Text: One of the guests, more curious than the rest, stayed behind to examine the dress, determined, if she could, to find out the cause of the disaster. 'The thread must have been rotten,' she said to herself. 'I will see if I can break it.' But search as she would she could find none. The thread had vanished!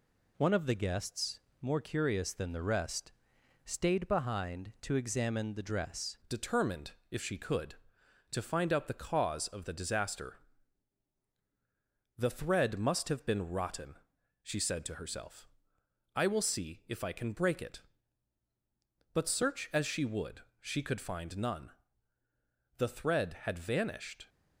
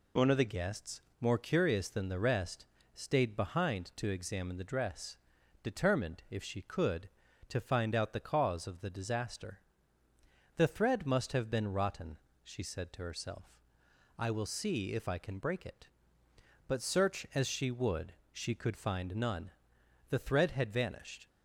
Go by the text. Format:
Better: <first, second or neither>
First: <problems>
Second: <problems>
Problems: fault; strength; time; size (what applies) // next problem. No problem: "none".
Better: second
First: changes voice at "determined"; from 6.2 s on; 18.0 s long // pauses between "would" and "she"; slight; at 20.4 s; 0.18 s long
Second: pauses between "would" and "she"; slight; at 18.1 s; 0.18 s long